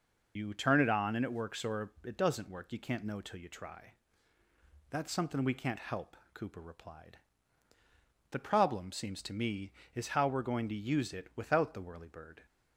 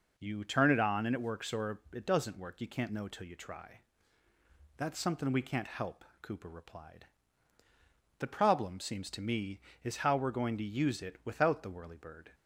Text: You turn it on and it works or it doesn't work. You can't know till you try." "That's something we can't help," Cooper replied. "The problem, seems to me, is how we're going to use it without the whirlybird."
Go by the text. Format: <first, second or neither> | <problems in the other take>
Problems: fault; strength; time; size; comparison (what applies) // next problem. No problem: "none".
second | loses the start of "You"; at 0.3 s; 70 ms